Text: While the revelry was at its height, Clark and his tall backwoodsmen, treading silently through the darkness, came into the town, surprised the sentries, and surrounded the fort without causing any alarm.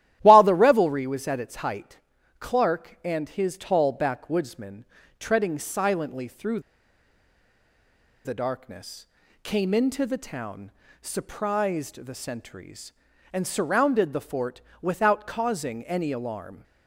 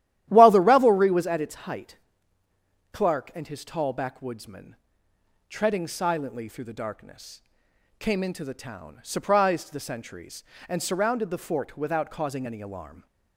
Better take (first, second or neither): second